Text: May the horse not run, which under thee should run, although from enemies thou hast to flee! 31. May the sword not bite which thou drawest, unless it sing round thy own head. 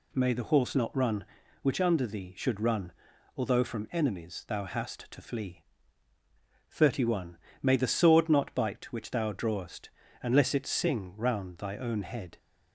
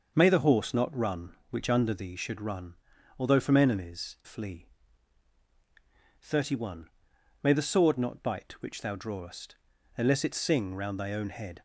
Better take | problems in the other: first | starts louder than the rest; until 1.1 s; 6 dB // skips "thou hast to"; at 4.2 s

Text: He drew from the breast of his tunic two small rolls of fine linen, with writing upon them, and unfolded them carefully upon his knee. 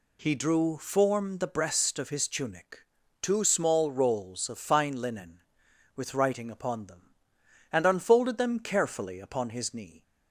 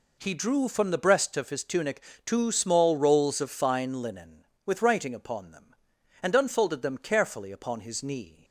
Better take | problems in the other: second | says "form" for "from"; at 0.7 s // pauses between "tunic" and "two"; at 2.8 s; 0.42 s long; slight in the second

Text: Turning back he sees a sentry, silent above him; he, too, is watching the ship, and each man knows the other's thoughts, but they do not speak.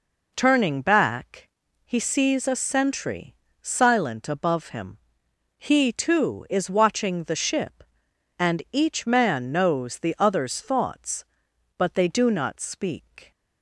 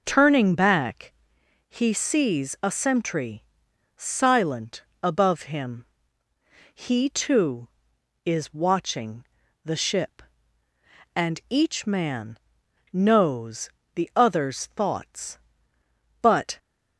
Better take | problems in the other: first | pauses between "back" and "he"; noticeable; at 1.1 s; 0.56 s long; slight in the first // pauses between "silent" and "above"; slight; at 4.8 s; 0.20 s long // pauses between "watching" and "the"; at 9.2 s; 0.40 s long // pauses between "man" and "knows"; noticeable; at 12.3 s; 0.56 s long // pauses between "knows" and "the"; slight; at 13.6 s; 0.24 s long // stops before "they do not speak"; at 16.5 s

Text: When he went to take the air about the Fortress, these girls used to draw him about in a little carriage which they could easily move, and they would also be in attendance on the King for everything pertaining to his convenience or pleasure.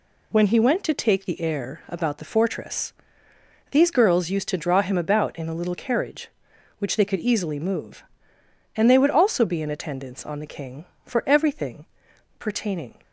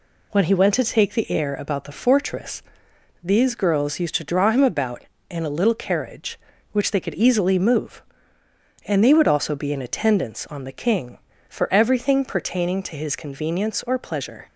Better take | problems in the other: second | pauses between "everything" and "pertaining"; noticeable; at 11.8 s; 0.54 s long // stops before "to his convenience or pleasure"; at 13.0 s

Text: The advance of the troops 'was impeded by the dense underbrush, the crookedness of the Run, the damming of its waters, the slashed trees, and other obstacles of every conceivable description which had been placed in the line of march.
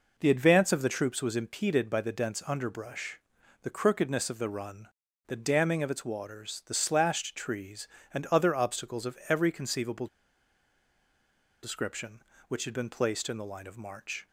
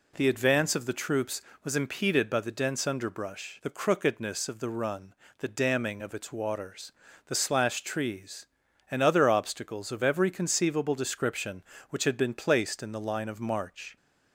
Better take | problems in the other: second | pauses between "conceivable" and "description"; strong; at 10.0 s; 1.5 s long

